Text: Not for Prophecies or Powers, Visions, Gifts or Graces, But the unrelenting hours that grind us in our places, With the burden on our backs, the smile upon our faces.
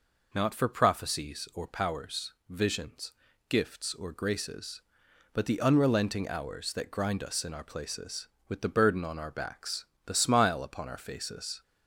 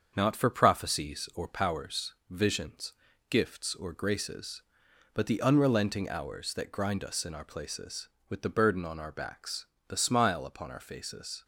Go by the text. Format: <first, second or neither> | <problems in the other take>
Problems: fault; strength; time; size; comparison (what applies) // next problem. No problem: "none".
first | gets quieter; noticeable; throughout; 5 dB